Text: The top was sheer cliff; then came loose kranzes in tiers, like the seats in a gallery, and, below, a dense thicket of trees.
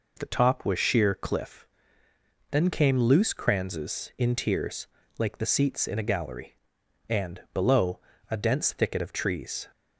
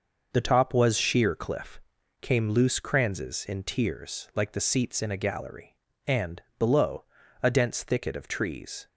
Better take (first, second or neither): first